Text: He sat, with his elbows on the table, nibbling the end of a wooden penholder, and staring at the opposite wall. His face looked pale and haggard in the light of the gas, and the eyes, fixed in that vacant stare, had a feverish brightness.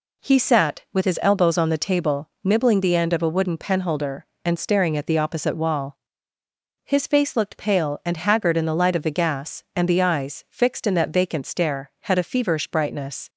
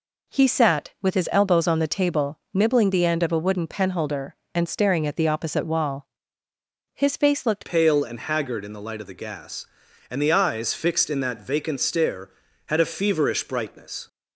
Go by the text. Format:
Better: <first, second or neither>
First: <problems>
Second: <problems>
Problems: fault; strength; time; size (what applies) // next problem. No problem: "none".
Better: first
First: none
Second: changes voice at "pale"; from 7.6 s on; 6.4 s long